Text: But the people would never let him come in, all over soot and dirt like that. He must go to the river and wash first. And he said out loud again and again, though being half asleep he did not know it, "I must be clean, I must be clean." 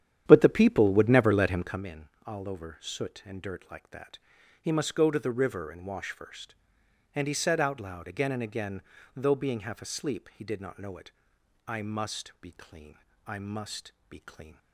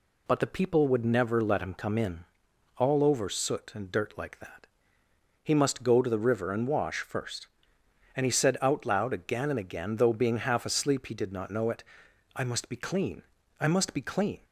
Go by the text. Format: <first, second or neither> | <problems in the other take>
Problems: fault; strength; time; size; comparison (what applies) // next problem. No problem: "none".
second | starts louder than the rest; strong; until 1.8 s; 10 dB // pauses between "must" and "be"; slight; at 13.9 s; 0.18 s long